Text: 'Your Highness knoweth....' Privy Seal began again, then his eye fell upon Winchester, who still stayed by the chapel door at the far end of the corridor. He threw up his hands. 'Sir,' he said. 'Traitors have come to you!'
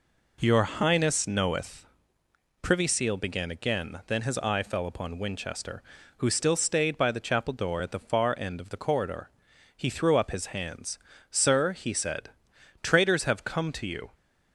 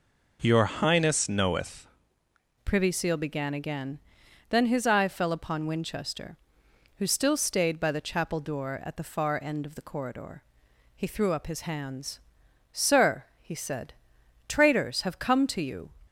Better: first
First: none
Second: changes voice at "Privy"; from 2.6 s on; 13.2 s long

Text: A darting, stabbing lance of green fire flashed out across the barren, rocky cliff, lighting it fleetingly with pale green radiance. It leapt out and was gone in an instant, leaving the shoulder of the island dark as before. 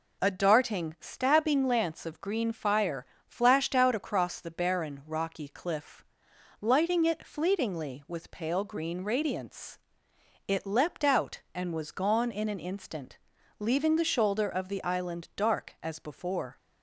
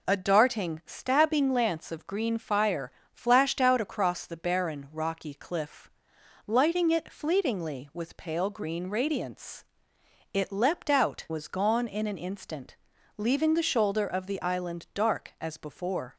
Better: first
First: pauses between "fire" and "flashed"; slight; at 3.0 s; 0.22 s long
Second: pauses between "fire" and "flashed"; slight; at 2.9 s; 0.22 s long // skips "and"; at 11.2 s

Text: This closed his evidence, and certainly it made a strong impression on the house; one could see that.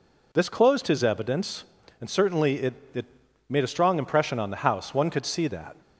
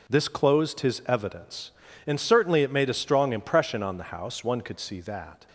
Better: second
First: says "it" twice; at 2.9 s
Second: none

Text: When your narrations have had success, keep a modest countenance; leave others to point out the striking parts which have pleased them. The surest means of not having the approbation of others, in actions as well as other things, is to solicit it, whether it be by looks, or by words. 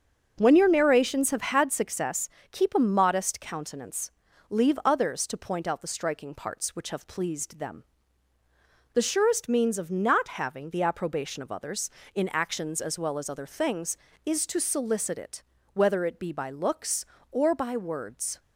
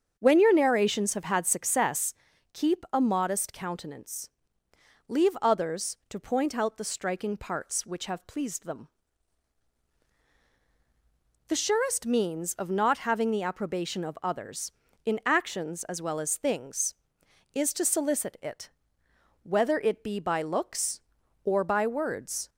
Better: first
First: starts louder than the rest; until 1.3 s; 6.5 dB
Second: starts louder than the rest; until 1.1 s; 7 dB // skips "other"; at 16.3 s

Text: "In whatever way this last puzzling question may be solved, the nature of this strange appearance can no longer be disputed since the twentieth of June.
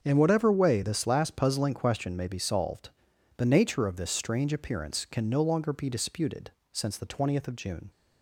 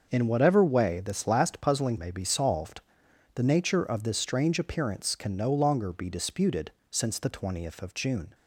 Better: first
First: starts louder than the rest; until 1.0 s; 6.5 dB // pauses between "disputed" and "since"; slight; at 6.5 s; 0.20 s long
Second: starts louder than the rest; noticeable; until 1.1 s; 6 dB // skips "question"; at 1.9 s // pauses between "disputed" and "since"; slight; at 6.7 s; 0.18 s long

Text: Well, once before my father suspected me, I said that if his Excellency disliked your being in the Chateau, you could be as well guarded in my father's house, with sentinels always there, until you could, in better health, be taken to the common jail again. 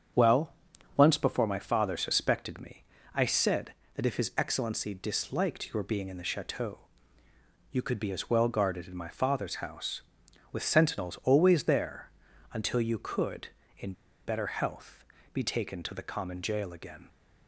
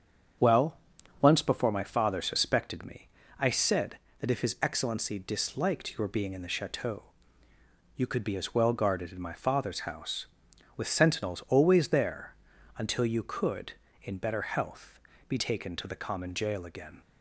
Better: second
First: starts louder than the rest; strong; until 1.5 s; 7.5 dB // pauses between "in" and "better"; slight; at 13.9 s; 0.32 s long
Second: starts louder than the rest; strong; until 1.8 s; 7.5 dB

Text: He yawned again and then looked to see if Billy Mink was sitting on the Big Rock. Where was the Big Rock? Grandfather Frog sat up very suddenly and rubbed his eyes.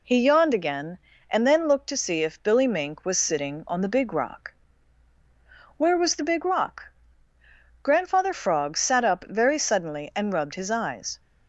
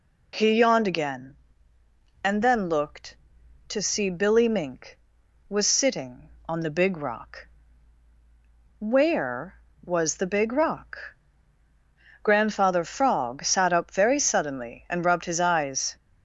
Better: first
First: none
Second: skips "if"; at 4.1 s

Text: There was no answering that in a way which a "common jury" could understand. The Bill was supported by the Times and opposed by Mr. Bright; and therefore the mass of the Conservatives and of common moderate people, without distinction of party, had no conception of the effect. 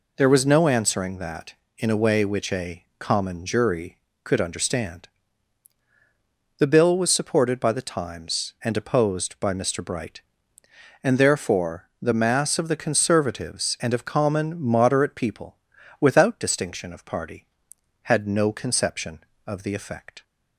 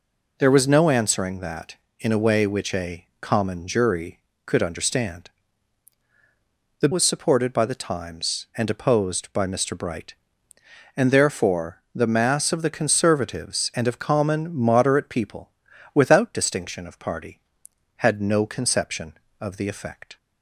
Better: first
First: none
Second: skips "Bill"; at 6.9 s

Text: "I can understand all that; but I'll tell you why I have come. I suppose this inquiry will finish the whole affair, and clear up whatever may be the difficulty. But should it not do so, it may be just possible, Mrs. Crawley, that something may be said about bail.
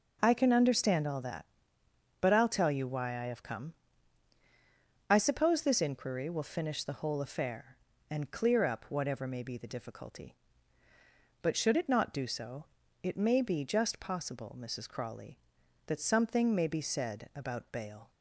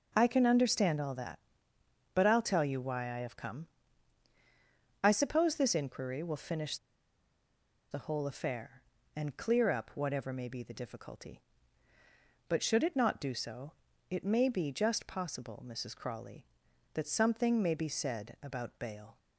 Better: first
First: none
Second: pauses between "finish" and "the"; at 6.7 s; 1.1 s long

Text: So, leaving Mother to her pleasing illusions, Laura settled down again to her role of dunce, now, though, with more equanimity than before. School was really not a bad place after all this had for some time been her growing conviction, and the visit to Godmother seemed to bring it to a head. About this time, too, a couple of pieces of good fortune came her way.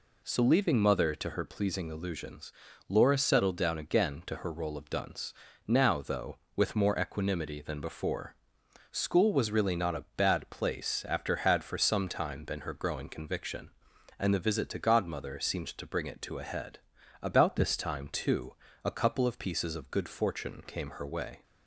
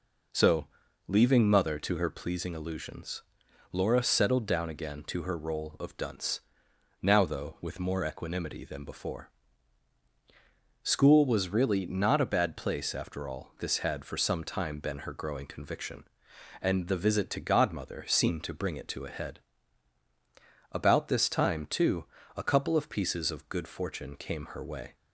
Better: second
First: skips "all this"; at 11.3 s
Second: none

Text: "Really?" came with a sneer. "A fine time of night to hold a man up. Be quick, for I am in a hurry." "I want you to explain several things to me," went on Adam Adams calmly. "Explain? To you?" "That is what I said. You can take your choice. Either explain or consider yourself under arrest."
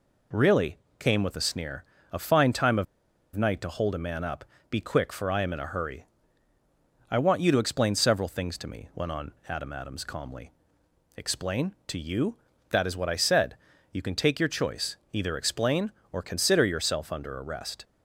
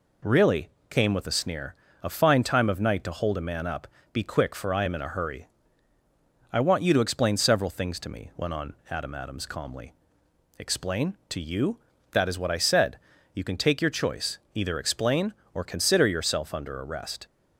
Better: second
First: pauses between "of" and "night"; noticeable; at 2.8 s; 0.50 s long // pauses between "on" and "Adam"; slight; at 9.3 s; 0.18 s long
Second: pauses between "on" and "Adam"; slight; at 8.7 s; 0.18 s long

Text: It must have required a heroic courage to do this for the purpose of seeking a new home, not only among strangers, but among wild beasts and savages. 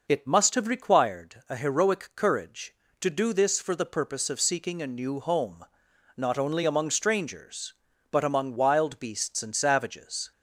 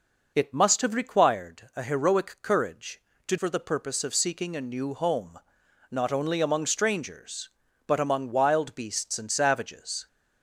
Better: first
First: none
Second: skips "do this"; at 3.3 s

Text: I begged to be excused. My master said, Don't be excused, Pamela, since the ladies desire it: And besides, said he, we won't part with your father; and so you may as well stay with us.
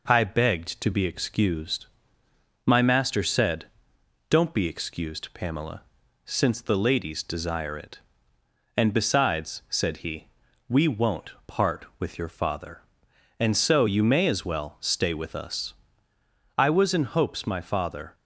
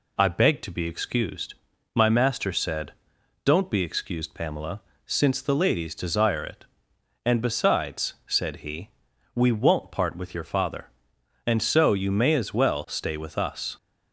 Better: second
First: pauses between "won't" and "part"; slight; at 11.3 s; 0.16 s long // goes on to say "I was in hopes my father"; from 16.5 s on; 1.5 s long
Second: none

